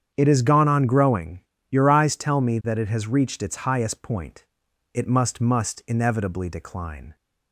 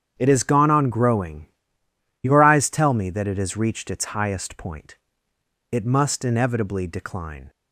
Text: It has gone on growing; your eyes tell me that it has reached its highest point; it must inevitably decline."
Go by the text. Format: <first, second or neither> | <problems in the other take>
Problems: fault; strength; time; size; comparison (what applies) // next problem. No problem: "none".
second | starts louder than the rest; strong; until 1.1 s; 8 dB; strong in the second // says "must" twice; at 5.4 s